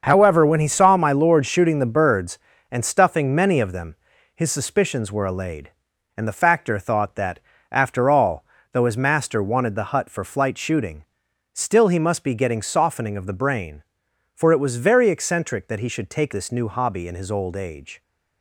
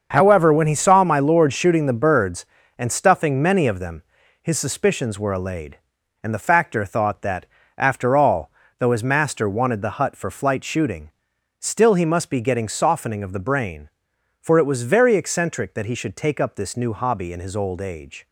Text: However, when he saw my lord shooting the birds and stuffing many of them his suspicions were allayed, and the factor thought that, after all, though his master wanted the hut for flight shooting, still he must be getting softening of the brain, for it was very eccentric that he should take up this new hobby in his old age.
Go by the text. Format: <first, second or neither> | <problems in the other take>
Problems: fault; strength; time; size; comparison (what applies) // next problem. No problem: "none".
second | starts louder than the rest; until 1.0 s; 6.5 dB; also in the second // pauses between "them" and "his"; at 3.9 s; 0.40 s long; also in the second // skips "up"; at 16.3 s